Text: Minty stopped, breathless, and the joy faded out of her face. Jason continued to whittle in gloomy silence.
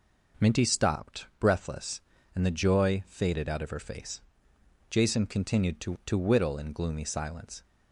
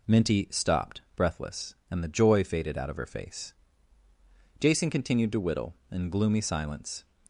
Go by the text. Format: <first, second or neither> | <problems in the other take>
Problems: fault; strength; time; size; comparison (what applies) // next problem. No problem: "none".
second | says "to" twice; at 6.0 s